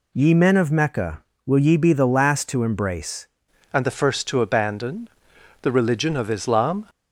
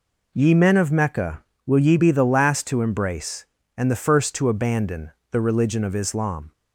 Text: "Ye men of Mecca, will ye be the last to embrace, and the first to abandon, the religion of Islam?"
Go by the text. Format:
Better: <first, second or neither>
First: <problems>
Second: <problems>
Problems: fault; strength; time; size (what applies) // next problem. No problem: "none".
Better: second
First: changes voice at "and"; from 3.7 s on; 3.1 s long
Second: none